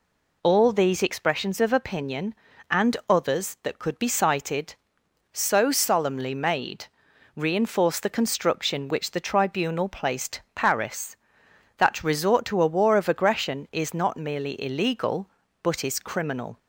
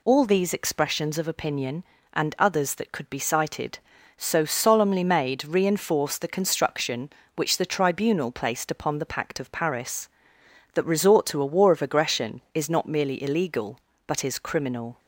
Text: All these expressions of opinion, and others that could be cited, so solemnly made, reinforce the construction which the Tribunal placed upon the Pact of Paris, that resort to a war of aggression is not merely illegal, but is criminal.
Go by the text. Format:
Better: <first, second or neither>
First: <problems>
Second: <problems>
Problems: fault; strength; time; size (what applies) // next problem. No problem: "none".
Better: second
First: skips "upon the Pact of"; at 10.4 s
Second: none